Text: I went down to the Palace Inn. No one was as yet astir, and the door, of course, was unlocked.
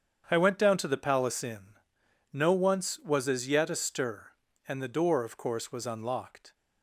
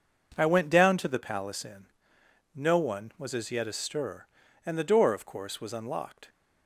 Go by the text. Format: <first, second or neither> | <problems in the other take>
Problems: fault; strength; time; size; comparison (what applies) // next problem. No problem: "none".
second | starts louder than the rest; strong; until 1.3 s; 8 dB // says "once" for "one"; at 2.5 s